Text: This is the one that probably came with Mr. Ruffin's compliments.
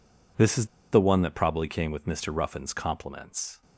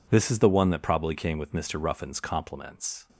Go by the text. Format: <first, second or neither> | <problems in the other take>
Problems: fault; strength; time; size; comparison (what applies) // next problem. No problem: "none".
second | pauses between "is" and "the"; slight; at 0.6 s; 0.25 s long